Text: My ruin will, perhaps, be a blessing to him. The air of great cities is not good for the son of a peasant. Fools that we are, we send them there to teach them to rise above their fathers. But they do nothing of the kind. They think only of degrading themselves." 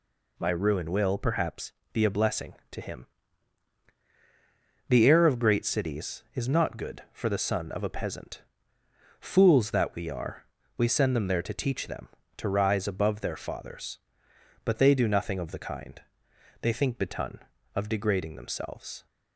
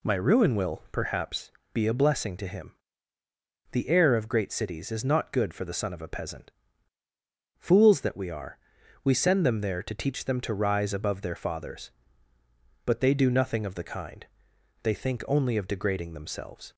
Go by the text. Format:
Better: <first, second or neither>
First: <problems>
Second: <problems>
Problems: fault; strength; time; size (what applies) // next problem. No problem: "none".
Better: second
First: says "betun" for "only"; at 16.9 s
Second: none